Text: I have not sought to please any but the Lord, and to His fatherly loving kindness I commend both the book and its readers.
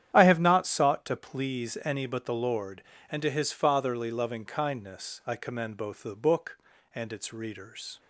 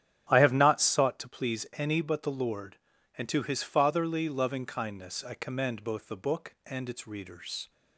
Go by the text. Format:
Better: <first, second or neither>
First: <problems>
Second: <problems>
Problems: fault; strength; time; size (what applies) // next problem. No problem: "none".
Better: neither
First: starts louder than the rest; strong; until 1.1 s; 10 dB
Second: starts louder than the rest; strong; until 1.3 s; 11 dB